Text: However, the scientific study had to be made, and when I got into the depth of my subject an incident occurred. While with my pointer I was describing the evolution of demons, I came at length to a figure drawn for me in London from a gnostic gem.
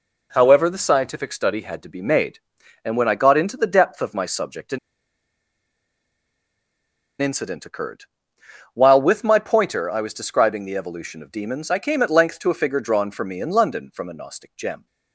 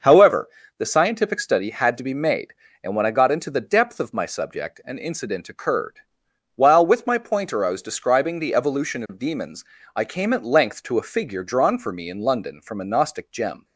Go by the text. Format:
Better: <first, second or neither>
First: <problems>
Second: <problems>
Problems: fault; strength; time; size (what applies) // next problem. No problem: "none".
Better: second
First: pauses between "an" and "incident"; strong; at 4.7 s; 2.4 s long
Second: none